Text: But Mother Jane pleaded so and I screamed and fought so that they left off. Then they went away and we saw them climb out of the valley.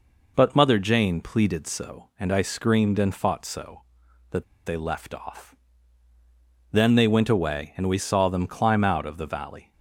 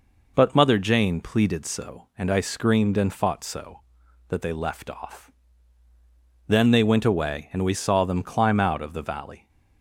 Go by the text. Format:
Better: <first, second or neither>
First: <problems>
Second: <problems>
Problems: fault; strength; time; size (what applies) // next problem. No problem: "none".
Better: second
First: pauses between "that" and "they"; slight; at 4.4 s; 0.22 s long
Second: none